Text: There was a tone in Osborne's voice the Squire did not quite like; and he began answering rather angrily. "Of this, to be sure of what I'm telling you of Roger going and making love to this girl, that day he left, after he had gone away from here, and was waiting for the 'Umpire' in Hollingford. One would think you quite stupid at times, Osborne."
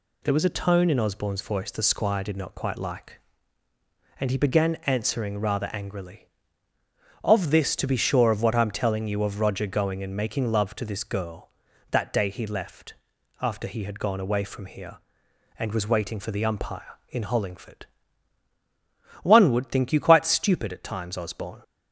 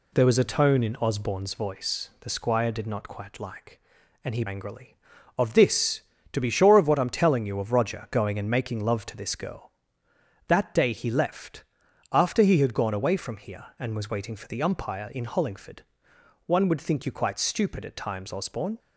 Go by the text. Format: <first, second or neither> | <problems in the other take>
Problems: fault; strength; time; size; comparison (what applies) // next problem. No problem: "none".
first | skips "began answering rather"; at 4.4 s